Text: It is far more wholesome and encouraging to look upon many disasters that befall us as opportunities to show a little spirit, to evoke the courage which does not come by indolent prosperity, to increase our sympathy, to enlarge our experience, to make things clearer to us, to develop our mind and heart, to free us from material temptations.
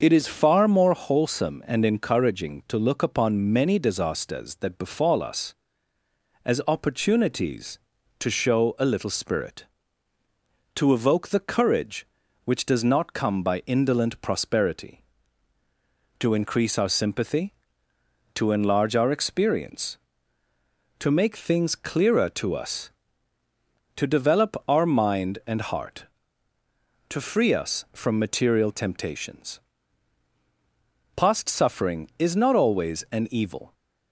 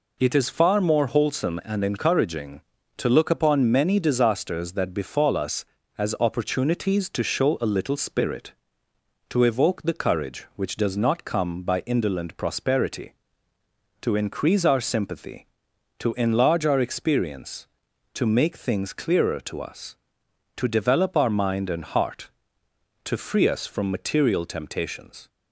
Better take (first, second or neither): second